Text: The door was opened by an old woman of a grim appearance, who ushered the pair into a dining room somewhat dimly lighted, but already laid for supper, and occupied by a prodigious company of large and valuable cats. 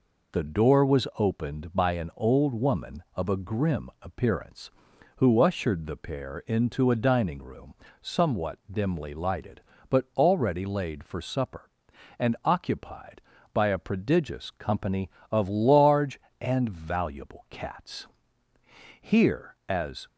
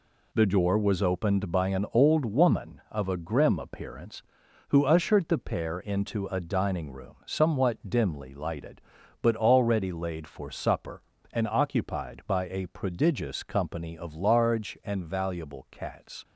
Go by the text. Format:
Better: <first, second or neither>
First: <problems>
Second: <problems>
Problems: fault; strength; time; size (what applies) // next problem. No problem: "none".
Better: second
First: pauses between "room" and "somewhat"; slight; at 7.7 s; 0.28 s long // goes on to say "Here as"; noticeable; from 19.0 s on; 1.0 s long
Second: none